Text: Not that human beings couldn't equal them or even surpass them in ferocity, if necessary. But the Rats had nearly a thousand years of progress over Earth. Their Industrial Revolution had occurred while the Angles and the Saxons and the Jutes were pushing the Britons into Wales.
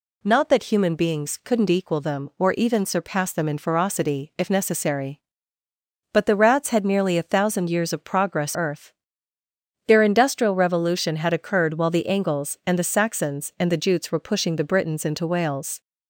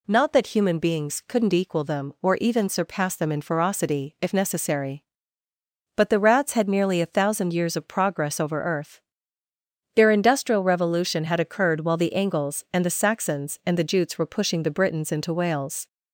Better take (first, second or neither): second